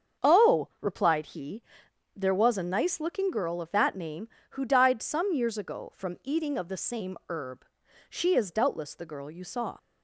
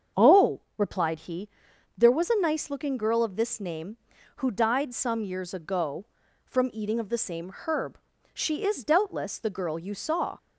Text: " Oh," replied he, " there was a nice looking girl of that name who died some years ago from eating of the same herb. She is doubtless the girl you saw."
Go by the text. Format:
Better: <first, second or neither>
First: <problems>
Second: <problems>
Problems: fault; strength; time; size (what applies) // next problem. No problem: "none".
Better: first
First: starts louder than the rest; until 1.3 s; 6.5 dB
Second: starts louder than the rest; strong; until 1.3 s; 7 dB // says "this" for "that"; at 3.3 s